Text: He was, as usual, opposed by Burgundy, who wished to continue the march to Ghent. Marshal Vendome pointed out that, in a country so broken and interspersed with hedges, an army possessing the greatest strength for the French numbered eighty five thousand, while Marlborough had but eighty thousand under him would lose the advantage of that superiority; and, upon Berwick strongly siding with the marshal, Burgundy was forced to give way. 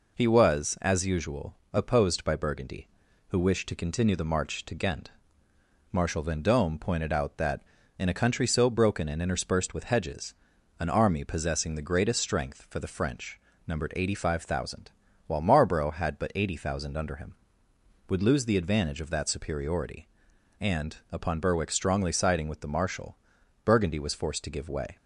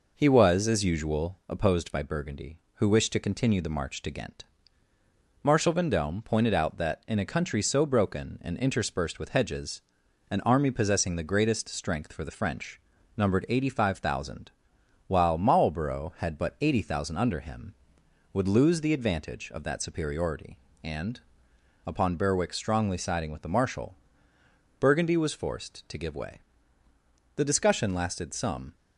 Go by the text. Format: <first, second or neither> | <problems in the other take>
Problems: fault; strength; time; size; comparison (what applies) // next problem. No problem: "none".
first | pauses between "French" and "numbered"; slight; at 12.8 s; 0.36 s long; slight in the first // goes on to say "The discussion lasted some"; from 27.3 s on; 1.4 s long